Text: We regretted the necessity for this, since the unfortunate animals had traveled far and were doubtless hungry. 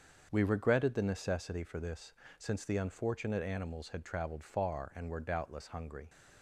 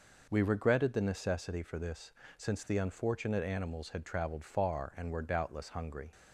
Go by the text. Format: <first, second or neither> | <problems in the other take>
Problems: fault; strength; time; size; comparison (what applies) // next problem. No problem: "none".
second | gets quieter; strong; throughout; 7.5 dB